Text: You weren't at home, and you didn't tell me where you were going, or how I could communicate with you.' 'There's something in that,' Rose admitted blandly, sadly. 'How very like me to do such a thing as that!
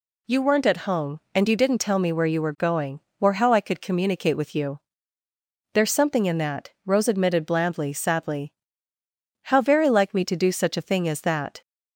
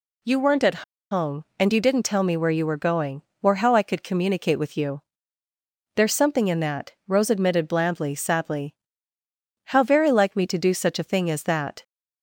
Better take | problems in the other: first | pauses between "at" and "home"; slight; at 0.8 s; 0.28 s long

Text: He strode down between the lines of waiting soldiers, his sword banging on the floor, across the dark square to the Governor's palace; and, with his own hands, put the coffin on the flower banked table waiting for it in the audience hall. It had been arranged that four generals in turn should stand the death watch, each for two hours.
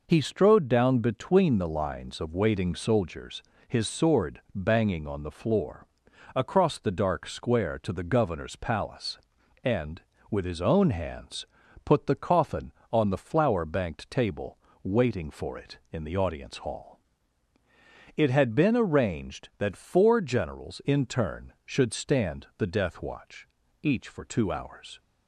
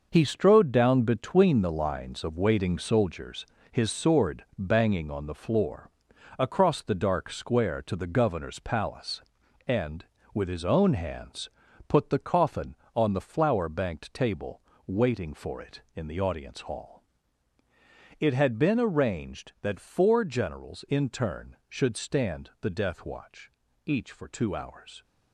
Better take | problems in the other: first | gets quieter; strong; throughout; 9 dB // pauses between "table" and "waiting"; slight; at 14.6 s; 0.26 s long; slight in the first

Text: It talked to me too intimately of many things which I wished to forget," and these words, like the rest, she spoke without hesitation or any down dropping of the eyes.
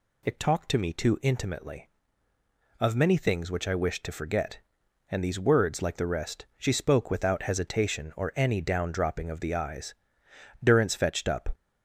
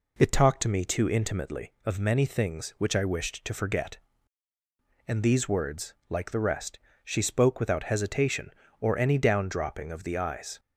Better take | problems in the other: second | goes on to say "Durrance fetched up"; noticeable; from 10.6 s on; 0.92 s long

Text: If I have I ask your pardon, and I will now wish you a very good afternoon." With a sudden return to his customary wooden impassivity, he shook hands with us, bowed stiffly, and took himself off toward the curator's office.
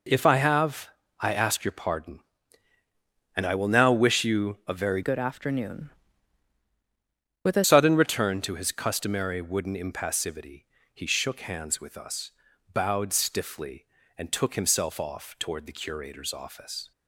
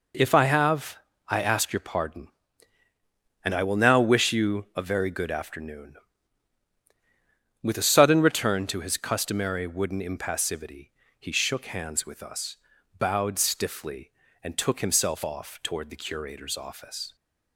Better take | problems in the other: second | pauses between "have" and "I"; slight; at 0.8 s; 0.32 s long; slight in the second // changes voice from "good" to "a"; from 5.0 to 7.6 s; 2.6 s long

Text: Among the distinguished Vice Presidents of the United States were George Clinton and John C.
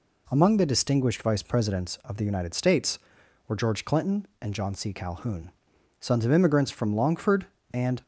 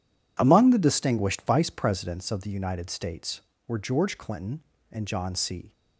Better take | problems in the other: second | goes on to say "Calhoun sons of immigrants from Longford and"; strong; from 4.9 s on; 3.1 s long

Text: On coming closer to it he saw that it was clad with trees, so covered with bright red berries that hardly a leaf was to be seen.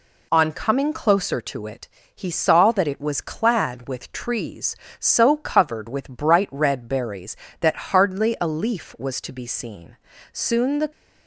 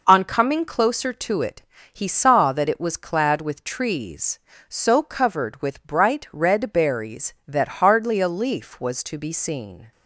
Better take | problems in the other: second | pauses between "it" and "he"; slight; at 1.8 s; 0.26 s long; slight in the second // goes on to say "Soon the"; from 10.3 s on; 0.58 s long

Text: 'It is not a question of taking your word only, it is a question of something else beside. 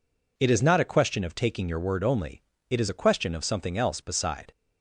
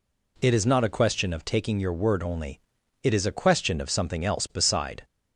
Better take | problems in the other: neither | none

